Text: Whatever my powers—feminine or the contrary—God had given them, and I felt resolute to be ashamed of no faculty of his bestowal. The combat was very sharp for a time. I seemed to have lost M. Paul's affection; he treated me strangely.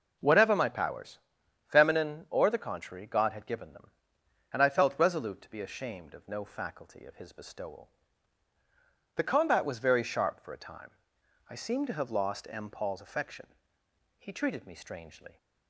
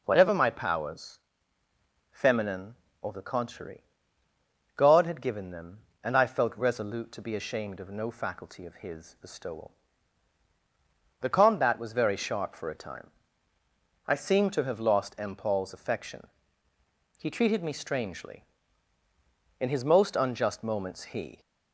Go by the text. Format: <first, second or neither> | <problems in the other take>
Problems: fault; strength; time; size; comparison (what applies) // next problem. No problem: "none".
first | goes on to say "In his most unjust moments he"; strong; from 19.5 s on; 1.8 s long